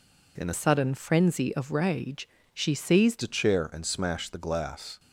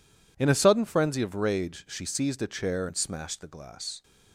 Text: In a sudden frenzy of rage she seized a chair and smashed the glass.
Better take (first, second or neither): second